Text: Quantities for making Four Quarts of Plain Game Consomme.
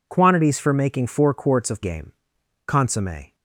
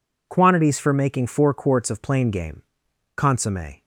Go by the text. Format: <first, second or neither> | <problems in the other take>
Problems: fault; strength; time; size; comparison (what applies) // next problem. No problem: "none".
second | skips "Plain"; at 1.8 s // pauses between "Game" and "Consomme"; noticeable; at 2.1 s; 0.54 s long; noticeable in the second